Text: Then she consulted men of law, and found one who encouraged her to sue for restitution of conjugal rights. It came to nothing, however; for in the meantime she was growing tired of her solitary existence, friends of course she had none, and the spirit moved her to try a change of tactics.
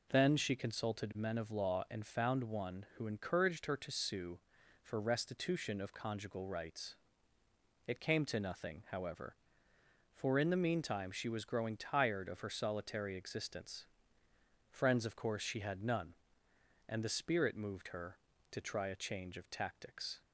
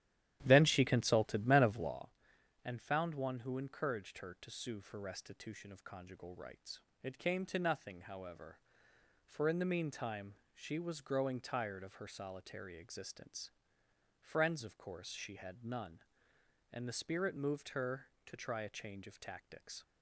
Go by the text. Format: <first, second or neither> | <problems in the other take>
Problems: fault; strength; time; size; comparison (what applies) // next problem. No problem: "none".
first | starts louder than the rest; strong; until 2.0 s; 12 dB // pauses between "meantime" and "she"; slight; at 10.3 s; 0.18 s long